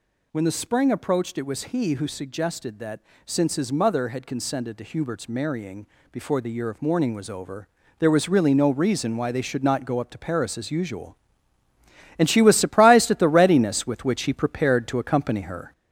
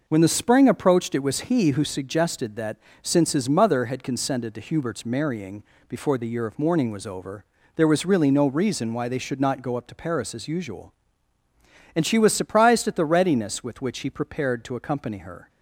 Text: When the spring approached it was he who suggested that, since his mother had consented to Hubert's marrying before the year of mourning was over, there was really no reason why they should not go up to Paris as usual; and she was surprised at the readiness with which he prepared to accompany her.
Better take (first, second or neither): second